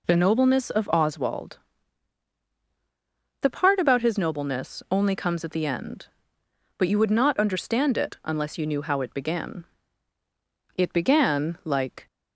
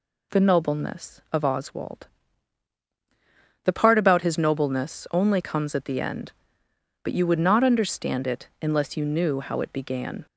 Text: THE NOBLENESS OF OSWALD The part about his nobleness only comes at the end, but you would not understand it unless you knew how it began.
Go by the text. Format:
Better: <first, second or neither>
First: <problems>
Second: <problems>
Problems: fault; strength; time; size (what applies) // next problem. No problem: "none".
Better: second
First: pauses between "OSWALD" and "The"; strong; at 1.5 s; 1.8 s long // goes on to say "It began like"; noticeable; from 10.7 s on; 1.3 s long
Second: pauses between "OSWALD" and "The"; strong; at 2.0 s; 1.5 s long